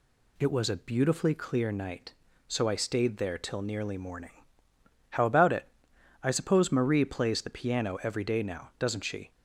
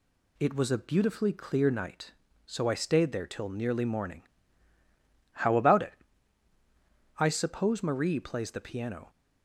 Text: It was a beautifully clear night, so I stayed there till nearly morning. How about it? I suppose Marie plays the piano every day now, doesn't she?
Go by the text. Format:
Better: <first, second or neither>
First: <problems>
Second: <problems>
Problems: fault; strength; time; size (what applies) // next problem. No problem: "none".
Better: first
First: none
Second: stops before "every day now doesn't she"; at 9.0 s